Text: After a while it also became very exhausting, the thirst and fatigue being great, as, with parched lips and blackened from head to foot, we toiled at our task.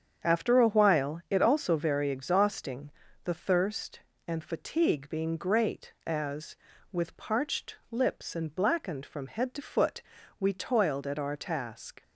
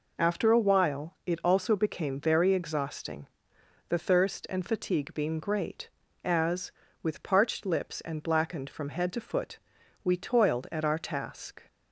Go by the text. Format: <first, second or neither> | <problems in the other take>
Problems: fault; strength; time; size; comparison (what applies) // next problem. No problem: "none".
second | starts louder than the rest; strong; until 1.3 s; 7.5 dB // skips "became"; at 1.7 s // pauses between "parched" and "lips"; slight; at 7.7 s; 0.16 s long